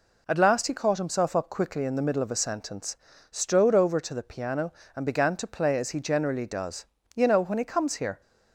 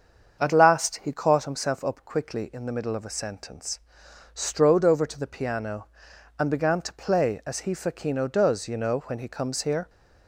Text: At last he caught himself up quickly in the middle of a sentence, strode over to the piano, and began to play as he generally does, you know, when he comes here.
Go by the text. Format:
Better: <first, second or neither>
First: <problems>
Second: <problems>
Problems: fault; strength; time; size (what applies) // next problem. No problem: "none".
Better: first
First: none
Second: starts louder than the rest; until 1.4 s; 7 dB // says "facchino" for "generally"; at 7.7 s